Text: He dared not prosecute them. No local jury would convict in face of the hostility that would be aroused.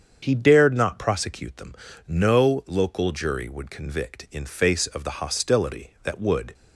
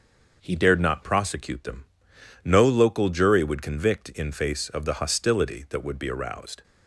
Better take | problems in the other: second | starts louder than the rest; strong; until 1.2 s; 7.5 dB; also in the second // stops before "be aroused"; at 6.5 s

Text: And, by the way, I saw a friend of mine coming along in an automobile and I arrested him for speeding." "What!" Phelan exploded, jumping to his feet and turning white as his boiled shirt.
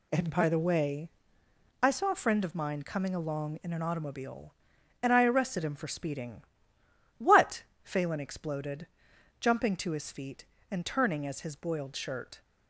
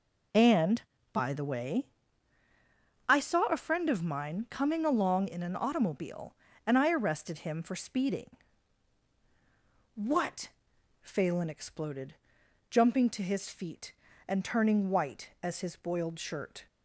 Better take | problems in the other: second | skips "white"; at 11.2 s

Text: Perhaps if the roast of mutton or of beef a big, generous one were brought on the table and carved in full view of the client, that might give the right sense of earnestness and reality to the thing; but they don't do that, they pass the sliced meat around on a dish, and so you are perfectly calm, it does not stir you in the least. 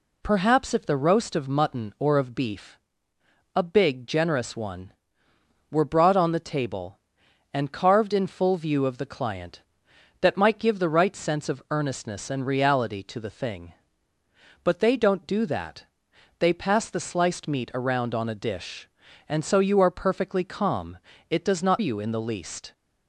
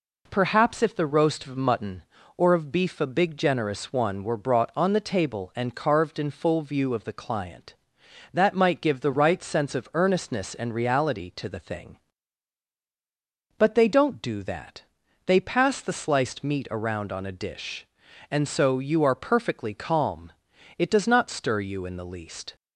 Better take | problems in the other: second | pauses between "beef" and "a"; noticeable; at 2.7 s; 0.78 s long // skips "stir"; at 21.7 s

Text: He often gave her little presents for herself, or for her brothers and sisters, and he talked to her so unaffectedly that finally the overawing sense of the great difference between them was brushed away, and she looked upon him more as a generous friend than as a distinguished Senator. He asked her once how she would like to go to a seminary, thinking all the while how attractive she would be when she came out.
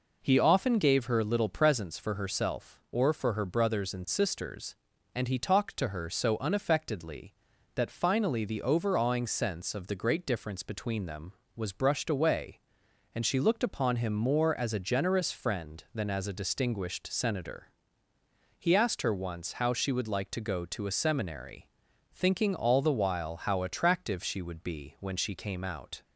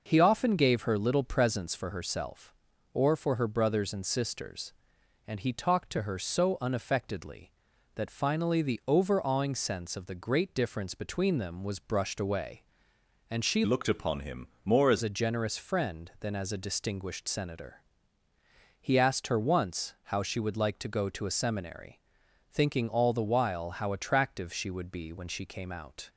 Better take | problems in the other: first | changes voice from "looked" to "as"; from 13.6 to 15.0 s; 1.4 s long // pauses between "him" and "more"; slight; at 14.4 s; 0.18 s long

